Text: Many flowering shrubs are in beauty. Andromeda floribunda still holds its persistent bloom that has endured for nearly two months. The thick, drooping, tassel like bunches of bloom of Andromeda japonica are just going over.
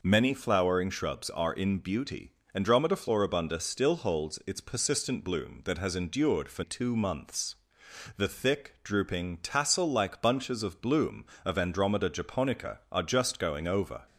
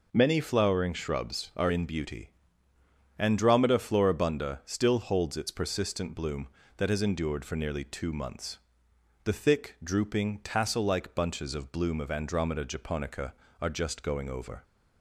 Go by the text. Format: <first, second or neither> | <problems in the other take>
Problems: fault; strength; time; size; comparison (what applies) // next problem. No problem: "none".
second | skips "nearly"; at 6.6 s